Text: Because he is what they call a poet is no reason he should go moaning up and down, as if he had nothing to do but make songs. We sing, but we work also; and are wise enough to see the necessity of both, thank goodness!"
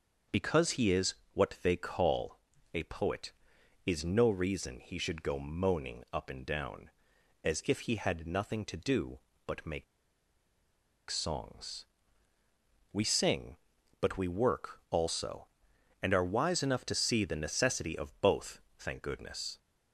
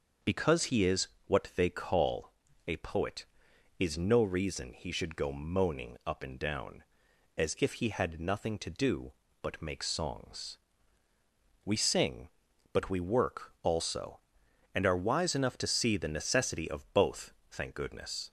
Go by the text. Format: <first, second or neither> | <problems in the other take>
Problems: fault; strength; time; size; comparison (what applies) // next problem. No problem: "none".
second | starts louder than the rest; until 1.4 s; 6 dB; also in the second // pauses between "is" and "what"; slight; at 1.1 s; 0.18 s long; slight in the second // pauses between "call" and "a"; slight; at 2.3 s; 0.36 s long; slight in the second // pauses between "make" and "songs"; strong; at 9.8 s; 1.2 s long